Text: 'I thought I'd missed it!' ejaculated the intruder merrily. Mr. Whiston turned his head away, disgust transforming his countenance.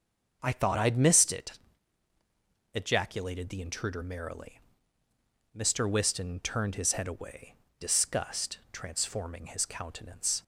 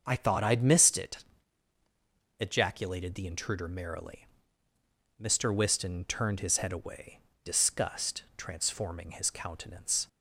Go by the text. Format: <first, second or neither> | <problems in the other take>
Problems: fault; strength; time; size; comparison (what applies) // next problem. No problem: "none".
neither | starts louder than the rest; the same in both